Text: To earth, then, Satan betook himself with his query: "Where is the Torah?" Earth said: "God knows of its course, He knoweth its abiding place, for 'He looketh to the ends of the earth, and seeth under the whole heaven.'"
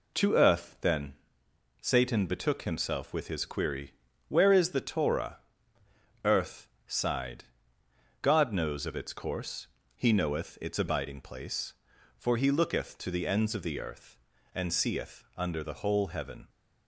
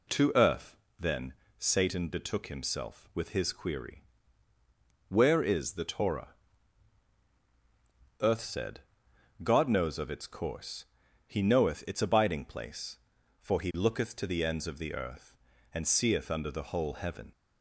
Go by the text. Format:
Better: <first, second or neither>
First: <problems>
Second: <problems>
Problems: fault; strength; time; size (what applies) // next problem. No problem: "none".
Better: second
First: says "sighed" for "said"; at 6.8 s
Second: none